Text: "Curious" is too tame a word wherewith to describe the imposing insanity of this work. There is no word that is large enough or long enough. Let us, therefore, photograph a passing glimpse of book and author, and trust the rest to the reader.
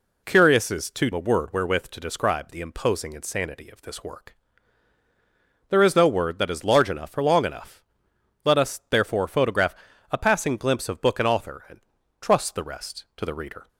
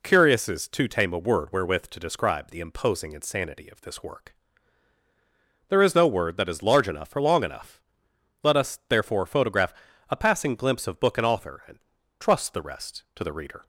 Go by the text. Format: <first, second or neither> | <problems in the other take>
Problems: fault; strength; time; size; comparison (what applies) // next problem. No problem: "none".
second | skips "tame"; at 1.1 s // pauses between "photograph" and "a"; slight; at 9.7 s; 0.34 s long; slight in the second // pauses between "and" and "trust"; at 11.7 s; 0.40 s long; also in the second